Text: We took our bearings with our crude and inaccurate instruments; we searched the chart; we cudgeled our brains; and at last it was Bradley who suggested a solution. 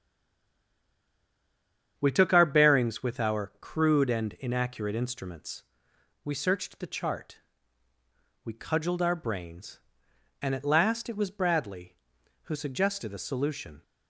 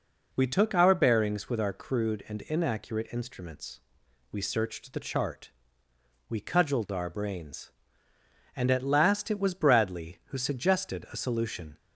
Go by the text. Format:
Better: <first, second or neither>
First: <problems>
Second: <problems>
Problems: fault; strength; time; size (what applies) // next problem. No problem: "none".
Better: second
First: stays silent before the first word; noticeable; until 1.9 s; 1.9 s long // starts louder than the rest; strong; until 2.9 s; 8.5 dB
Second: none